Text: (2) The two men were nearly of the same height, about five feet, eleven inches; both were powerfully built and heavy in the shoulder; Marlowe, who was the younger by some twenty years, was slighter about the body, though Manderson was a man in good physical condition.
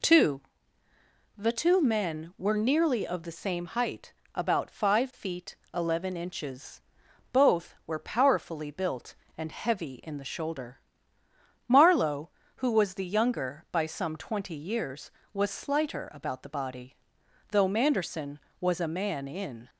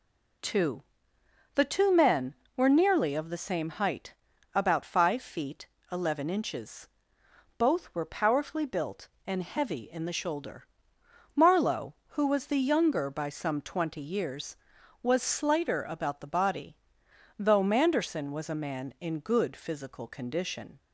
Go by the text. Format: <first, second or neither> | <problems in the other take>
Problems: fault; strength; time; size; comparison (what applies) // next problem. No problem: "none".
second | stops before "good physical condition"; at 19.6 s